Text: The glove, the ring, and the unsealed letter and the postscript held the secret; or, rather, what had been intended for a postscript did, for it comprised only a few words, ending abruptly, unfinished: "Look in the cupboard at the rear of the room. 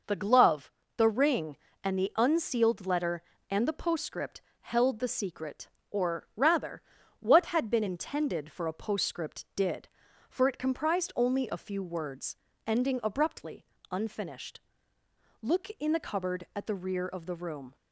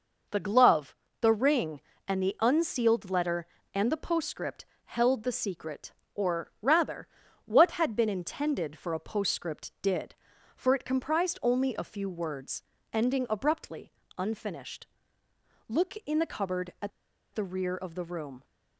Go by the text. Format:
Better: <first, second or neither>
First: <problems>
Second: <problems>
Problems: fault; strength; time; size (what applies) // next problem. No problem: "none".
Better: first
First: pauses between "postscript" and "held"; slight; at 4.4 s; 0.18 s long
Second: pauses between "postscript" and "held"; slight; at 4.6 s; 0.18 s long // pauses between "at" and "the"; at 16.9 s; 0.43 s long